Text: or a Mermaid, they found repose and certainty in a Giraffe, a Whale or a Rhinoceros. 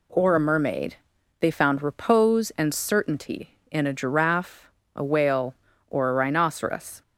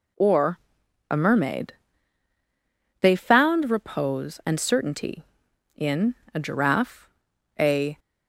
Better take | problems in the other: first | pauses between "or" and "a"; noticeable; at 0.5 s; 0.52 s long // pauses between "in" and "a"; slight; at 6.1 s; 0.18 s long // stops before "Whale or a Rhinoceros"; at 7.9 s

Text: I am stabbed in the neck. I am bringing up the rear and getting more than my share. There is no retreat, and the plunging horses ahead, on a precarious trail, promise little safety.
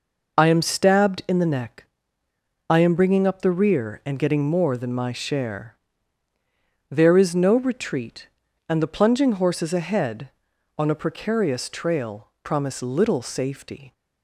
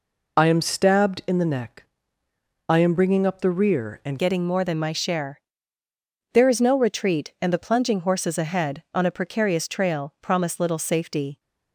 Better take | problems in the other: first | changes voice at "getting"; from 4.1 s on; 7.2 s long

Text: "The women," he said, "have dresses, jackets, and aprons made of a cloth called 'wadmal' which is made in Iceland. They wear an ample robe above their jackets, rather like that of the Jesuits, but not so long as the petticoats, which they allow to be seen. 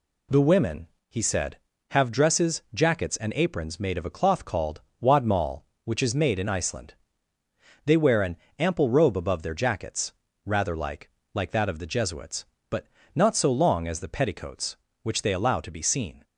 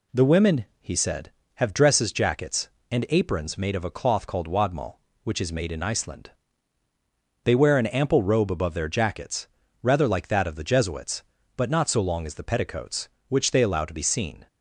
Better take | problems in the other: second | pauses between "called" and "wadmal"; slight; at 4.7 s; 0.22 s long // pauses between "an" and "ample"; slight; at 8.3 s; 0.24 s long // says "like" twice; at 11.3 s // pauses between "but" and "not"; slight; at 12.8 s; 0.30 s long

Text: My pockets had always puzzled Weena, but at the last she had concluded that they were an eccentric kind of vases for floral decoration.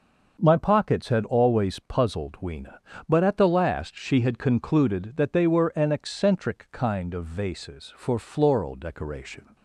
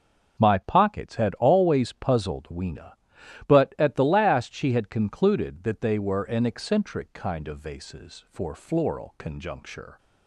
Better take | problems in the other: first | starts louder than the rest; until 1.4 s; 6.5 dB // says "conjuncture" for "decoration"; at 9.1 s

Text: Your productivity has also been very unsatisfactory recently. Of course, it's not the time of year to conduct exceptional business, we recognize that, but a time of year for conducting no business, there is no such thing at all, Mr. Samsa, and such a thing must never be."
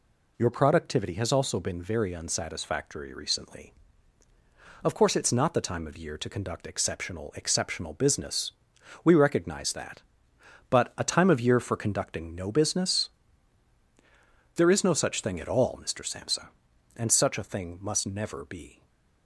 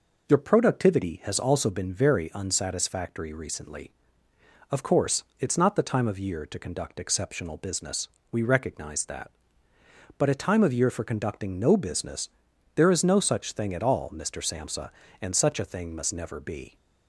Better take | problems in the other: second | says "exceptional" twice; at 7.3 s // stays silent after the last word; slight; from 18.7 s on; 0.5 s long

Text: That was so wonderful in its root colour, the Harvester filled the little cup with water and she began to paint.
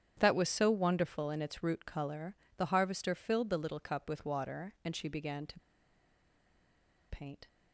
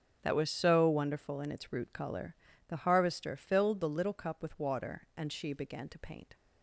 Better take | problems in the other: second | starts louder than the rest; strong; until 1.2 s; 9.5 dB; strong in the second // pauses between "to" and "paint"; strong; at 5.5 s; 1.5 s long

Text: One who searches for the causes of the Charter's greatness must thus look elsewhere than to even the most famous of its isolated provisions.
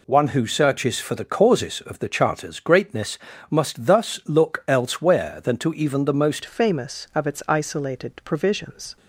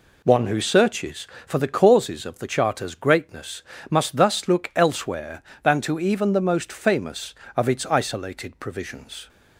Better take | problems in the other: second | pauses between "greatness" and "must"; slight; at 3.1 s; 0.32 s long; slight in the second // changes voice at "famous"; from 6.4 s on; 2.5 s long

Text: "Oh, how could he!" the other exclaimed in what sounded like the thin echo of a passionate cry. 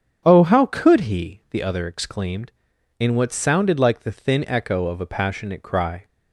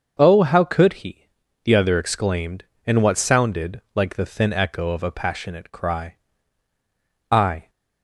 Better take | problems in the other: first | starts louder than the rest; until 1.1 s; 6.5 dB; strong in the first // goes on to say "I"; slight; from 7.3 s on; 0.38 s long

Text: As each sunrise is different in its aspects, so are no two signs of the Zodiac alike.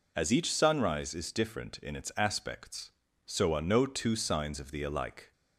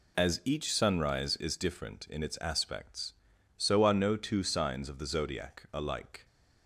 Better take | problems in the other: second | skips "Zodiac"; at 4.8 s

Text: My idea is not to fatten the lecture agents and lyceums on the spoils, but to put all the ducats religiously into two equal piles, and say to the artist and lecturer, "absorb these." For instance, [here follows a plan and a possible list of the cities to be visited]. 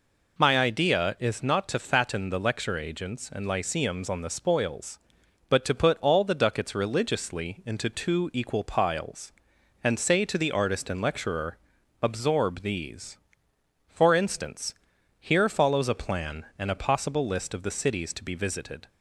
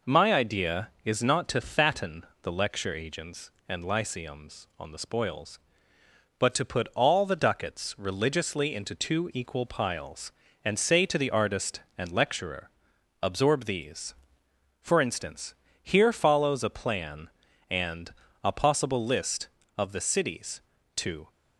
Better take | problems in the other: first | pauses between "fatten" and "the"; slight; at 2.2 s; 0.18 s long // pauses between "and" and "a"; slight; at 18.1 s; 0.30 s long // stops before "be visited"; at 21.3 s

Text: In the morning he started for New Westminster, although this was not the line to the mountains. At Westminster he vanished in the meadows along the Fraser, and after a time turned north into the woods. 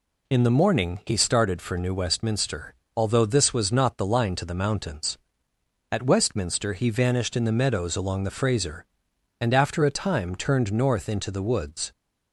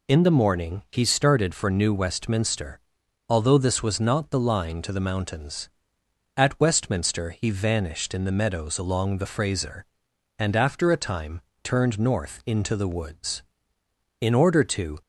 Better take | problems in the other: first | pauses between "time" and "turned"; slight; at 11.4 s; 0.22 s long // goes on to say "In order to"; noticeable; from 14.1 s on; 0.82 s long

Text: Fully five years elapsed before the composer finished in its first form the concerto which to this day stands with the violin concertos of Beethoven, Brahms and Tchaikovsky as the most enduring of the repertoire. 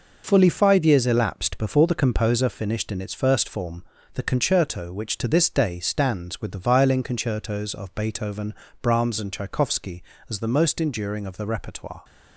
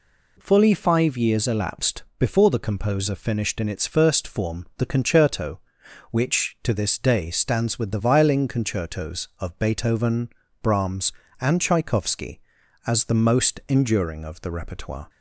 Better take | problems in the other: second | gets quieter; strong; throughout; 7.5 dB // pauses between "form" and "the"; slight; at 3.8 s; 0.32 s long

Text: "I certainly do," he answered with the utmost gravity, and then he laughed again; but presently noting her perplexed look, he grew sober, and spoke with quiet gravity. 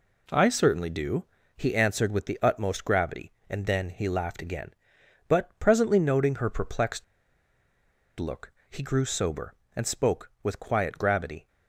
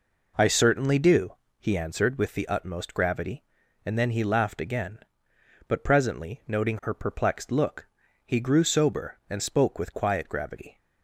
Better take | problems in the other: second | pauses between "perplexed" and "look"; at 7.0 s; 1.1 s long

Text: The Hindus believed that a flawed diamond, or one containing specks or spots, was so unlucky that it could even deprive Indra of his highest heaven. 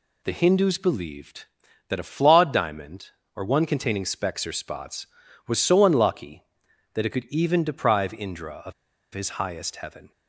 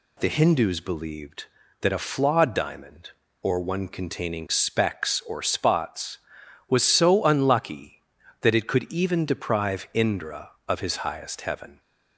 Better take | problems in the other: second | pauses between "of" and "his"; at 8.7 s; 0.42 s long

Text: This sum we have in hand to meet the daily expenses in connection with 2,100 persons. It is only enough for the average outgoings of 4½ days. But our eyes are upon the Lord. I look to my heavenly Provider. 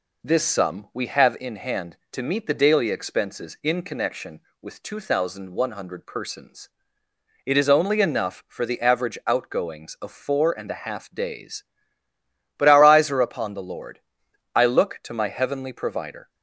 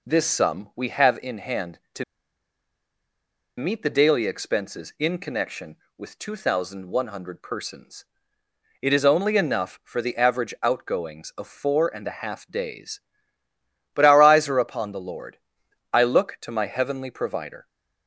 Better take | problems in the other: first | pauses between "to" and "meet"; strong; at 2.0 s; 1.5 s long

